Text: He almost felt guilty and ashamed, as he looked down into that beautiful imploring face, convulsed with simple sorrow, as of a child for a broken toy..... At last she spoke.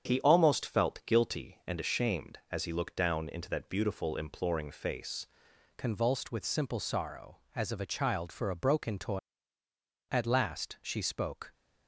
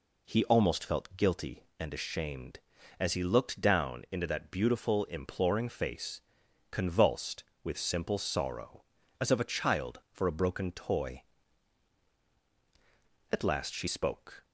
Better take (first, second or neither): second